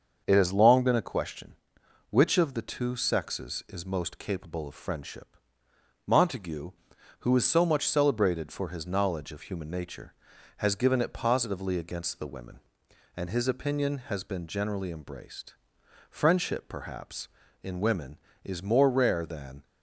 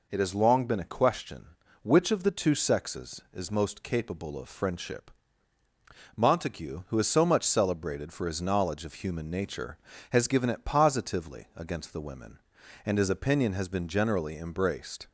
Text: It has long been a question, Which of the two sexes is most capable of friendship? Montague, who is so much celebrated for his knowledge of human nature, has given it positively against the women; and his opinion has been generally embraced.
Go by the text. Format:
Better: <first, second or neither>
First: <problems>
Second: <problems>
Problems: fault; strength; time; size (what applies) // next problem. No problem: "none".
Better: second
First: starts louder than the rest; until 1.2 s; 6.5 dB // goes on to say "Friendship perhaps in women is more rare than"; strong; from 16.0 s on; 3.5 s long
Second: none